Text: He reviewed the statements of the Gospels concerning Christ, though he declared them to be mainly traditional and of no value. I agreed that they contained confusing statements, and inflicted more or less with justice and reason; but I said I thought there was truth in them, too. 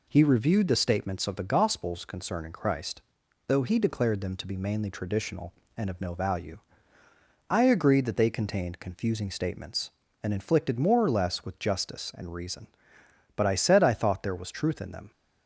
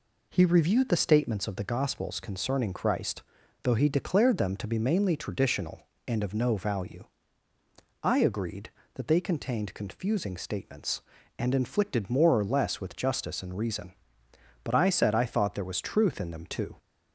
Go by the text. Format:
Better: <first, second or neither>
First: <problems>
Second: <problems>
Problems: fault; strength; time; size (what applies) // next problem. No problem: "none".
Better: second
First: stops before "too"; at 15.1 s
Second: none